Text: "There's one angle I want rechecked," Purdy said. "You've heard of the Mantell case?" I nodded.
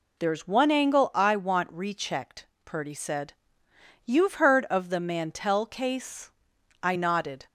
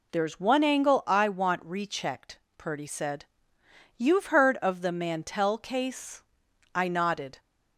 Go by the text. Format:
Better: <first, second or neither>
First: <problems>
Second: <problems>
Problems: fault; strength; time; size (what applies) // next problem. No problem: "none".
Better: neither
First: none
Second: none